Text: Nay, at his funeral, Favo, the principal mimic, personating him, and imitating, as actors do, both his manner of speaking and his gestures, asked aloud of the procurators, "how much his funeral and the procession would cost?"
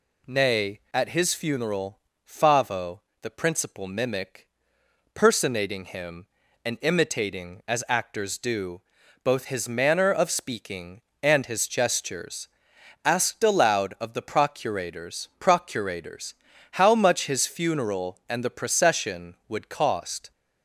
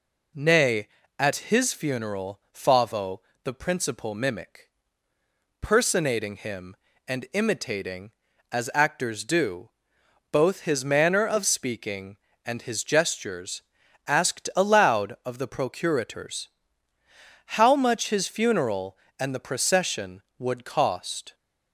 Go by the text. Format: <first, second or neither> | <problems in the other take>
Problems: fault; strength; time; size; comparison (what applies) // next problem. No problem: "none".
second | says "procurators" twice; at 15.3 s